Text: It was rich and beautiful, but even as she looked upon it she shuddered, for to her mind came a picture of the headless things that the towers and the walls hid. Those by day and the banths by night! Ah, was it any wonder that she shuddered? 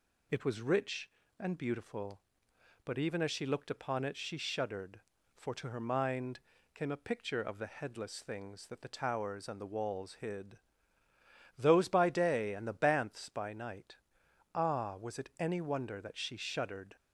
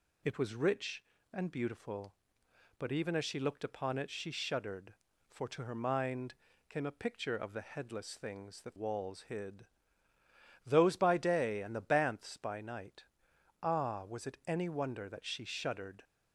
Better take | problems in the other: first | pauses between "mind" and "came"; slight; at 6.3 s; 0.36 s long; slight in the first // skips "the towers and the"; at 8.7 s

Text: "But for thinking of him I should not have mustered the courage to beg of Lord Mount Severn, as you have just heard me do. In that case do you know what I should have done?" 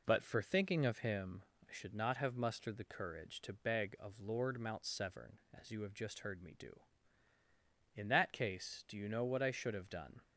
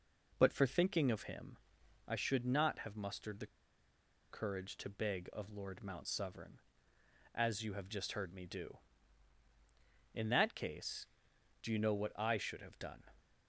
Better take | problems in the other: first | pauses between "him" and "I"; noticeable; at 1.5 s; 0.50 s long; slight in the first // pauses between "the" and "courage"; noticeable; at 3.4 s; 0.84 s long

